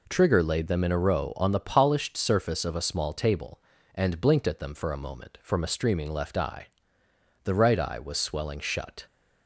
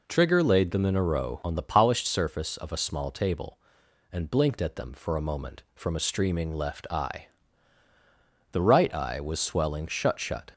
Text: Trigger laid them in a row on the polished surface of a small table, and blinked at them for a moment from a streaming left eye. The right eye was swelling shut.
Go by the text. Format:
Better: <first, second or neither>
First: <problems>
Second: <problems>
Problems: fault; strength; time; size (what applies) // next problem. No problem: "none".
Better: first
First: none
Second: says "shut" twice; at 10.1 s